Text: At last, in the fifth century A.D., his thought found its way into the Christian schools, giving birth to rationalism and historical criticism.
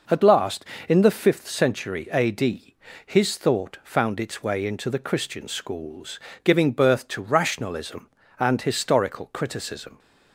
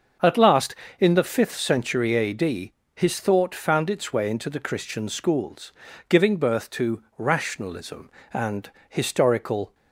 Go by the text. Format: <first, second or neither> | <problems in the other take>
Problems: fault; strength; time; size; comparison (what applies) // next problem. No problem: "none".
first | starts louder than the rest; until 1.4 s; 6.5 dB // pauses between "and" and "historical"; slight; at 8.7 s; 0.18 s long // stops before "criticism"; at 9.7 s